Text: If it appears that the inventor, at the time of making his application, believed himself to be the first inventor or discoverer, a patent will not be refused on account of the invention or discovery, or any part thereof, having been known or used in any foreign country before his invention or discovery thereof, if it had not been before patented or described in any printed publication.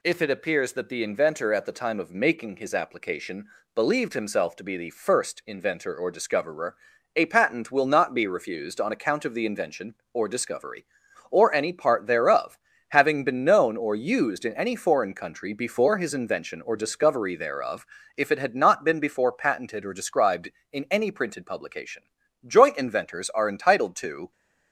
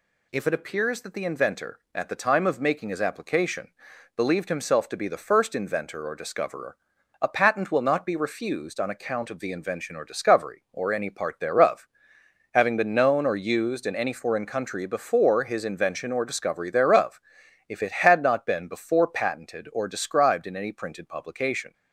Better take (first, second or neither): second